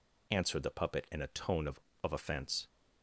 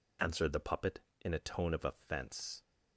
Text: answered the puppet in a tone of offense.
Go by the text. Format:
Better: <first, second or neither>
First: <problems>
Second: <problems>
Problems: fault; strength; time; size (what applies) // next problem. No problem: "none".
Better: second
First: says "of" twice; at 2.0 s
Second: none